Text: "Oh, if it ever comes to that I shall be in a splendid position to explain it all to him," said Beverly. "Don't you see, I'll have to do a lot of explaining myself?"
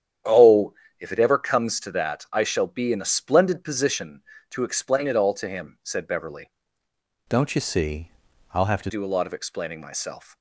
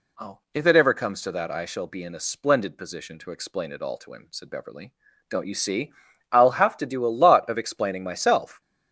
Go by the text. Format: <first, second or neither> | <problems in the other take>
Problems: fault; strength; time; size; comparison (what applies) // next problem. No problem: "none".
second | starts louder than the rest; strong; until 1.5 s; 9.5 dB // changes voice from "Don't" to "to"; from 7.2 to 8.9 s; 1.7 s long